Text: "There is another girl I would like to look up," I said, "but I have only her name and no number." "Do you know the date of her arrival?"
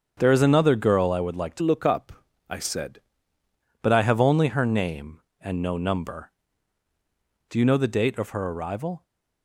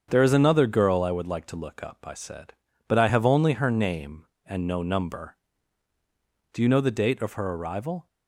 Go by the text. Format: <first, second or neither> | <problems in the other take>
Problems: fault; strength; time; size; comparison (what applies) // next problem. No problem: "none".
second | starts louder than the rest; strong; until 1.1 s; 7.5 dB; strong in the second // changes voice from "look" to "said"; from 1.6 to 2.9 s; 1.3 s long